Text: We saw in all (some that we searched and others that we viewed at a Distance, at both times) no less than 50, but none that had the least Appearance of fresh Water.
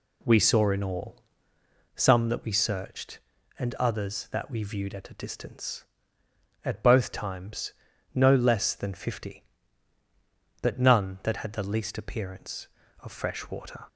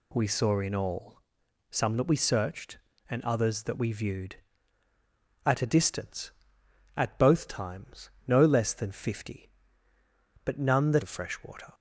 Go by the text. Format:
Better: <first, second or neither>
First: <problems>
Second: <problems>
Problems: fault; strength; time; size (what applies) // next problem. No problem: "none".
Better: first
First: none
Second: skips "had the least Appearance"; at 11.0 s